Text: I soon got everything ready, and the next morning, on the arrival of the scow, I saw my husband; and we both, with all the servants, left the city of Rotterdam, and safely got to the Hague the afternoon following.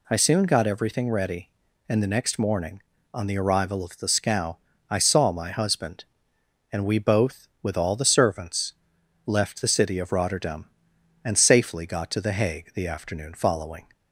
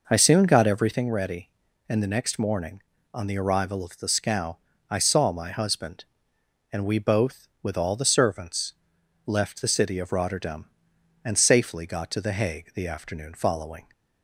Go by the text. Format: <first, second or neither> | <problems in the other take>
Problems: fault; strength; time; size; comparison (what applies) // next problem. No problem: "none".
first | starts louder than the rest; noticeable; until 1.1 s; 5 dB